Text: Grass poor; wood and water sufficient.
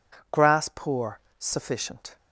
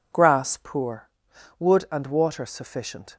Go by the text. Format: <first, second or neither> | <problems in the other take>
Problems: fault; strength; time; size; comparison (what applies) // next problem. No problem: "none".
second | skips "wood and water"; at 1.2 s